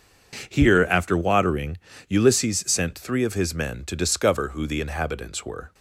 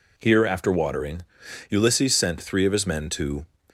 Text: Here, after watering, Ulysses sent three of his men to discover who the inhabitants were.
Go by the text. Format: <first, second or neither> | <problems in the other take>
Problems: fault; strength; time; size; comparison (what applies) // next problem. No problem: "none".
first | stops before "discover who the inhabitants were"; at 3.6 s